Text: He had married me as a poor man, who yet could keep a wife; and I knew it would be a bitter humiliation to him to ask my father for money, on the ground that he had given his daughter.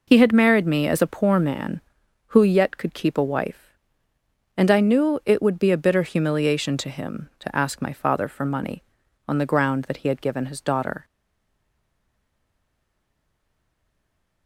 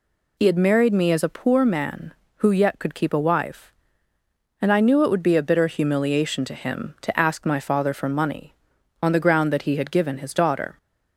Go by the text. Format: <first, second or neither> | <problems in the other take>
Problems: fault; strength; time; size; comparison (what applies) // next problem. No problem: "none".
second | stays silent after the last word; strong; from 11.0 s on; 3.4 s long